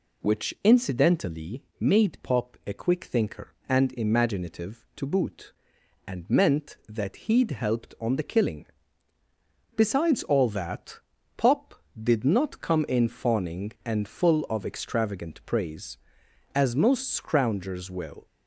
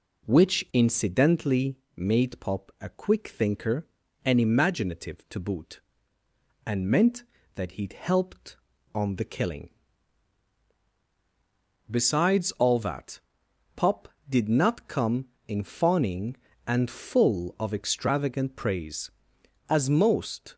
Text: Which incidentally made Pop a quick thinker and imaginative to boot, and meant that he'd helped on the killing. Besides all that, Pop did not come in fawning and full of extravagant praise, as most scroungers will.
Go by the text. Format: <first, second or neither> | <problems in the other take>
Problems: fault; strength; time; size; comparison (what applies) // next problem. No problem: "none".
first | pauses between "incidentally" and "made"; slight; at 1.7 s; 0.18 s long; slight in the first // stops before "scroungers will"; at 20.5 s